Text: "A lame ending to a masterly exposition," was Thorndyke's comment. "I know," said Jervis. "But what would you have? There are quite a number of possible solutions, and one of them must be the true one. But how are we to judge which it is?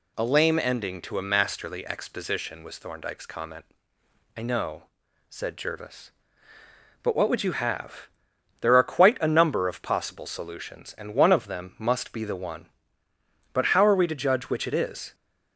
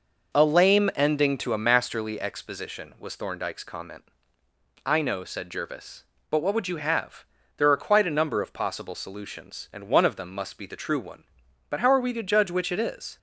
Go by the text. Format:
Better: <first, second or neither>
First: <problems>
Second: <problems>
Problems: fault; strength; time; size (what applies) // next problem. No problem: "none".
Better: second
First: skips "true"; at 12.3 s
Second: none